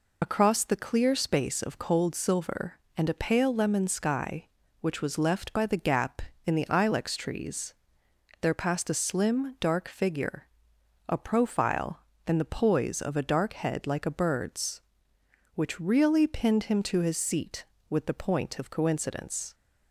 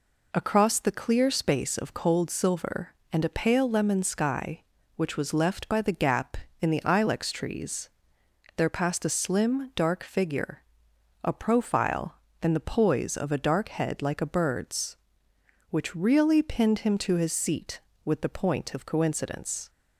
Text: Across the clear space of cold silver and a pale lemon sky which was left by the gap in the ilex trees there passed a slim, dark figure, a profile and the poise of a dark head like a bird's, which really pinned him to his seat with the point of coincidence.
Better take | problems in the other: second | loses the start of "Across"; at 0.2 s; 35 ms // pauses between "trees" and "there"; noticeable; at 7.7 s; 0.70 s long; noticeable in the second

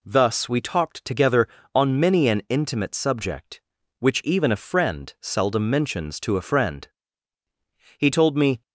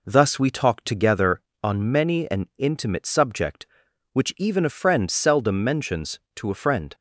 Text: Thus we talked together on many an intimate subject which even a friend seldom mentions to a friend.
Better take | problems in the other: second | goes on to say "He told me"; noticeable; from 7.9 s on; 0.64 s long

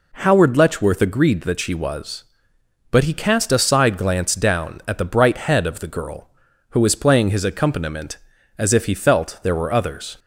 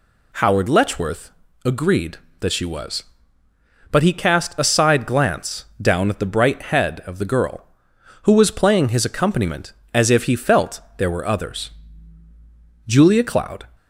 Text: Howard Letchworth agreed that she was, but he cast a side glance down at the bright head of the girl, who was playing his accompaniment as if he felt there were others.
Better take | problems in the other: first | pauses between "Letchworth" and "agreed"; slight; at 1.2 s; 0.34 s long // pauses between "glance" and "down"; slight; at 5.6 s; 0.16 s long // pauses between "felt" and "there"; slight; at 10.7 s; 0.18 s long // goes on to say "Julia Cloud"; noticeable; from 12.8 s on; 0.80 s long

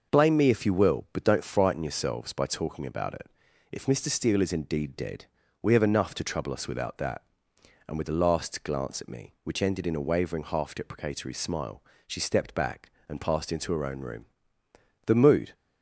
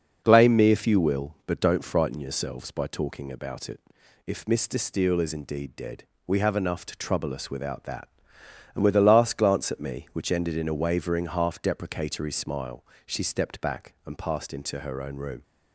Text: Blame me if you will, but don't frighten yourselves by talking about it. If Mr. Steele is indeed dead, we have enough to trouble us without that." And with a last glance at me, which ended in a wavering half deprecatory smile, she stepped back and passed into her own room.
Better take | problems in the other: second | goes on to say "The mood"; slight; from 15.0 s on; 0.48 s long

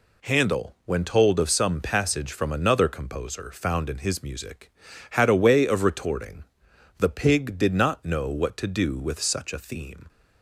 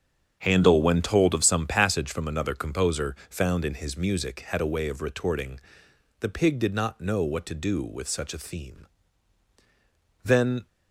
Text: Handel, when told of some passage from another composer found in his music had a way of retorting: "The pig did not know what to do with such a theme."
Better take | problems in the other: first | starts louder than the rest; strong; until 1.4 s; 7.5 dB // pauses between "composer" and "found"; slight; at 3.1 s; 0.16 s long // goes on to say "Then"; slight; from 10.2 s on; 0.44 s long

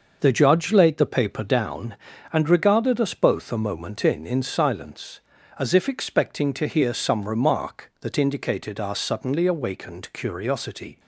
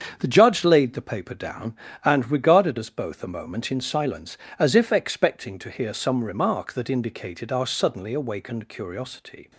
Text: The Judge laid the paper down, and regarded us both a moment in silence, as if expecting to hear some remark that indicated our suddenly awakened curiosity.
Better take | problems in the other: second | starts louder than the rest; noticeable; until 1.2 s; 6 dB; strong in the second // says "in" twice; at 4.2 s

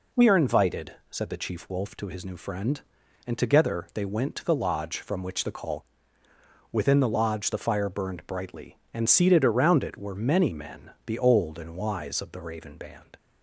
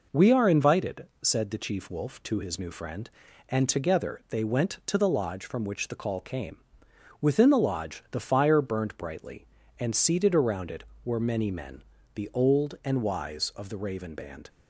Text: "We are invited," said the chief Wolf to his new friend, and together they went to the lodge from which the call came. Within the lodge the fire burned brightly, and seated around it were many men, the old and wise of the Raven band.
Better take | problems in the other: second | skips "came"; at 6.2 s

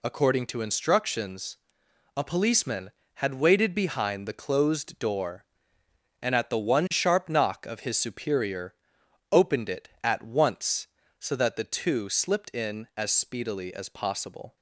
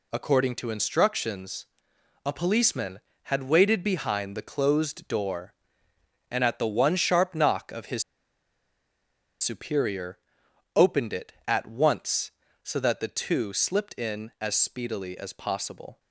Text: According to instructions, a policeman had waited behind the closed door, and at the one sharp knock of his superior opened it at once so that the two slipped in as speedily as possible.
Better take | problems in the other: first | pauses between "his" and "superior"; strong; at 8.0 s; 1.3 s long // pauses between "superior" and "opened"; noticeable; at 10.1 s; 0.58 s long; noticeable in the first

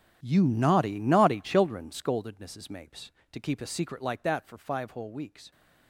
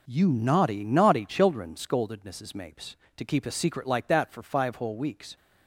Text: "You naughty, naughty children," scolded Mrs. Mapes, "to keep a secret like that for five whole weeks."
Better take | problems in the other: second | gets quieter; strong; throughout; 16 dB

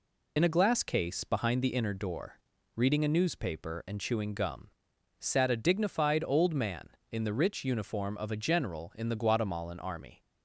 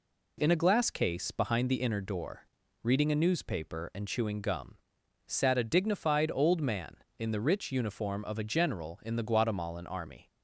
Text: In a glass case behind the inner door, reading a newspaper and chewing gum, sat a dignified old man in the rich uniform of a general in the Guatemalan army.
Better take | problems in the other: second | loses the start of "In"; at 0.3 s; 55 ms

